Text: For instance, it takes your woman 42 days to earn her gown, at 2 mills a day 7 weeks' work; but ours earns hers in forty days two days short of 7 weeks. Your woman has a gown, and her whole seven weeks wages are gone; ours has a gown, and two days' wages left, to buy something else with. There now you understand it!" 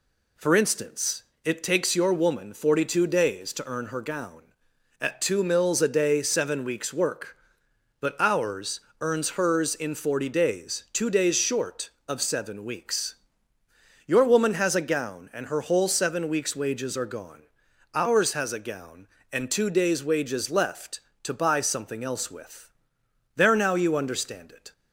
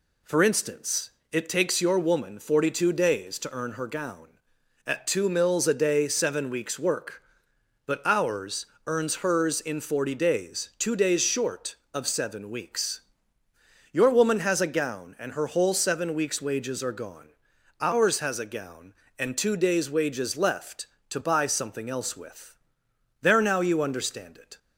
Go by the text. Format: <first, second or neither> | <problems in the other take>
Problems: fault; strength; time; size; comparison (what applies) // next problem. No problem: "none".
neither | pauses between "ours" and "earns"; slight; the same in both